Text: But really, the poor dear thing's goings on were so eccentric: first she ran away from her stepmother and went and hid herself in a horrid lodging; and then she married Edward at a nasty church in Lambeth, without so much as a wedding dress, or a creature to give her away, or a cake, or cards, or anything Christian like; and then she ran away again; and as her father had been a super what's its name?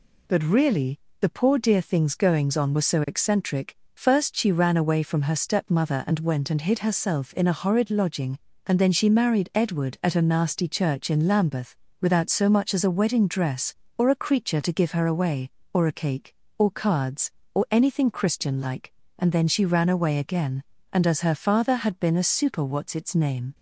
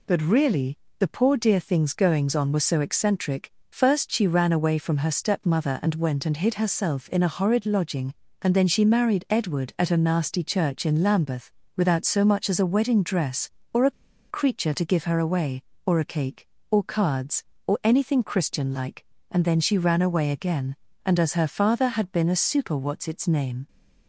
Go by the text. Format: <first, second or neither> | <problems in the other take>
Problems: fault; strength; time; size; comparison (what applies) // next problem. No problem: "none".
first | pauses between "a" and "creature"; at 13.9 s; 0.40 s long